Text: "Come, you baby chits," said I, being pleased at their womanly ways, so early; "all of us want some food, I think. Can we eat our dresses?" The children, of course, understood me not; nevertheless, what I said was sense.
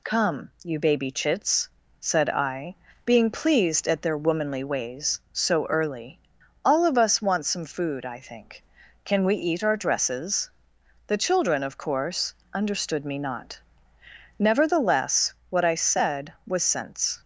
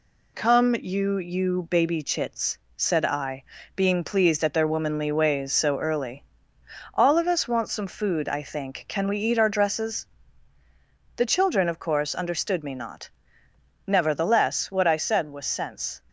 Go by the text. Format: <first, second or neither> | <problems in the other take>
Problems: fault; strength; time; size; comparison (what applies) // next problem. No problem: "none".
first | says "you" twice; at 1.1 s